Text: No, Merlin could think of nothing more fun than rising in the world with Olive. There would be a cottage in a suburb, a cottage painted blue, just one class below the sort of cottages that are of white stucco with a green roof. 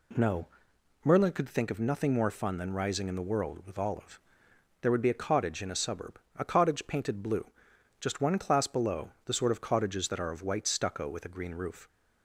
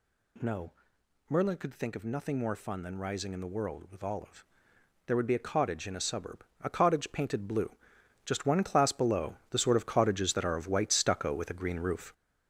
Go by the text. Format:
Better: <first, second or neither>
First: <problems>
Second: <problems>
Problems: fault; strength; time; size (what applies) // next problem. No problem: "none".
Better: first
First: none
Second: gets louder; throughout; 7 dB